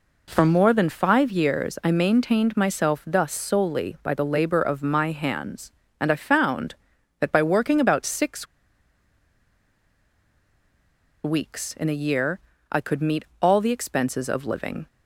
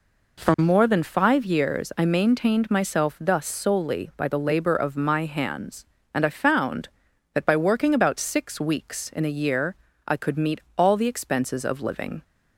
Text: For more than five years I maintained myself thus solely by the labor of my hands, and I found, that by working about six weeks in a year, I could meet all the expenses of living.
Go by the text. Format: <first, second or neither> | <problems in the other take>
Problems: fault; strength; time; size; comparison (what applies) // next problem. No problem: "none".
second | pauses between "six" and "weeks"; strong; at 8.4 s; 2.7 s long // pauses between "meet" and "all"; slight; at 13.2 s; 0.16 s long; slight in the second